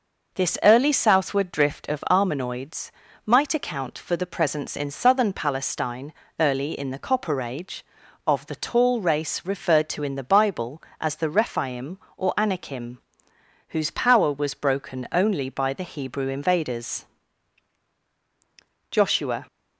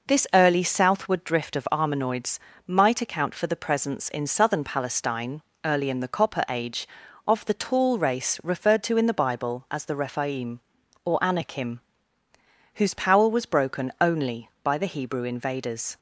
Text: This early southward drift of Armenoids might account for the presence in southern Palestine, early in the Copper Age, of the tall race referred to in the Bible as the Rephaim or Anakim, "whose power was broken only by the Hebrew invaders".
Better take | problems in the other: second | pauses between "Armenoids" and "might"; slight; at 2.9 s; 0.34 s long; slight in the second // goes on to say "Joshua"; from 18.9 s on; 0.54 s long

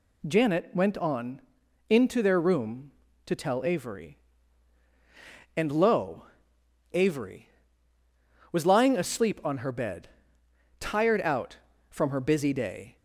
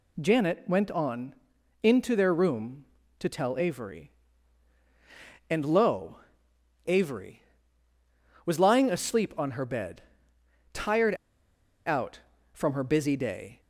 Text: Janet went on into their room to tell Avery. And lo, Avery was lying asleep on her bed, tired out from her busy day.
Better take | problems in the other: first | pauses between "on" and "into"; noticeable; at 1.3 s; 0.50 s long; noticeable in the first // pauses between "tired" and "out"; noticeable; at 11.1 s; 0.70 s long

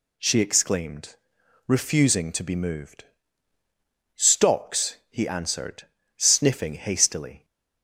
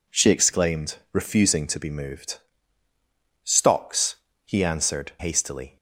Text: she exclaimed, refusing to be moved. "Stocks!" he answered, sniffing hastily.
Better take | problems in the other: first | skips "sniffing"; at 5.1 s

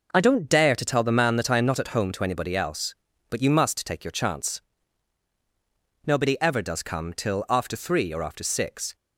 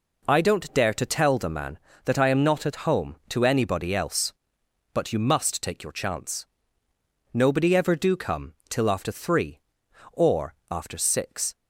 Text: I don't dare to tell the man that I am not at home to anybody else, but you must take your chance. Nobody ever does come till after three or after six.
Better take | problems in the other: first | says "do" for "does"; at 7.9 s // pauses between "come" and "till"; slight; at 8.5 s; 0.16 s long // pauses between "or" and "after"; slight; at 10.5 s; 0.16 s long

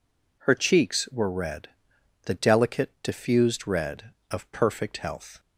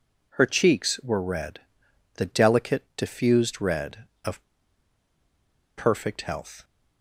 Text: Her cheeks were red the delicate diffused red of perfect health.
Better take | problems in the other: first | pauses between "red" and "the"; noticeable; at 1.5 s; 0.56 s long; noticeable in the first // pauses between "of" and "perfect"; strong; at 4.4 s; 1.3 s long

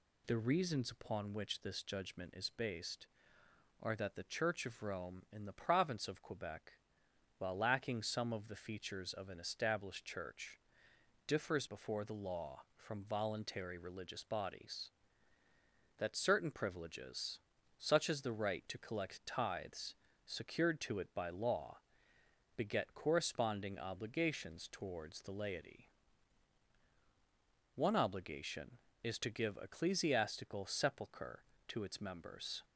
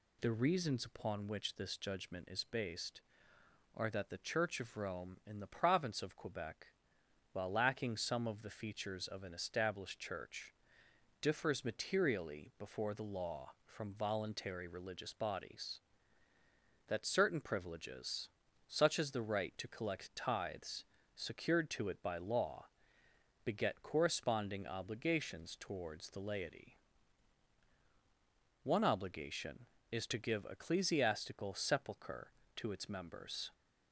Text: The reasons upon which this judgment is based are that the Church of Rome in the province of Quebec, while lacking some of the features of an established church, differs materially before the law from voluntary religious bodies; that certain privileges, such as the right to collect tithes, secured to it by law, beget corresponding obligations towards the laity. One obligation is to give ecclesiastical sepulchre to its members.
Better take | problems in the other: second | skips "materially"; at 11.6 s

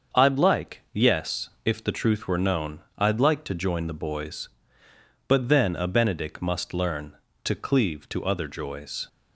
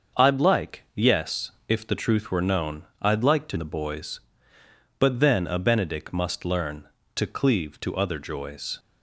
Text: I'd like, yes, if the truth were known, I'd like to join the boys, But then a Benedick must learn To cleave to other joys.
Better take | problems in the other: first | starts louder than the rest; until 1.2 s; 6.5 dB; also in the first // skips "join"; at 3.5 s

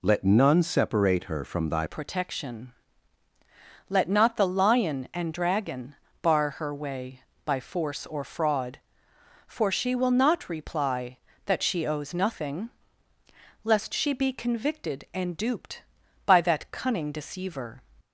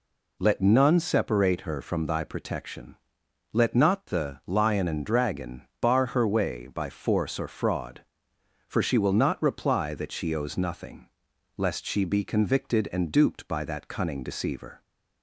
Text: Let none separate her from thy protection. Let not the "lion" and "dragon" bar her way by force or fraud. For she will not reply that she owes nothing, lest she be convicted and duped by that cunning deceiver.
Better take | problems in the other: second | changes voice at "protection"; from 1.8 s on; 16.0 s long // pauses between "dragon" and "bar"; slight; at 5.9 s; 0.26 s long; slight in the second

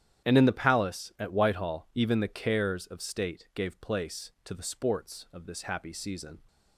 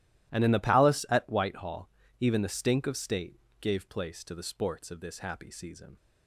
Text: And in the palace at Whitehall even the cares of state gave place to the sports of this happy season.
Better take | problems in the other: first | starts louder than the rest; strong; until 1.3 s; 14 dB; strong in the first // pauses between "Whitehall" and "even"; slight; at 1.8 s; 0.34 s long // says "stink" for "cares"; at 2.4 s // pauses between "state" and "gave"; slight; at 3.3 s; 0.22 s long

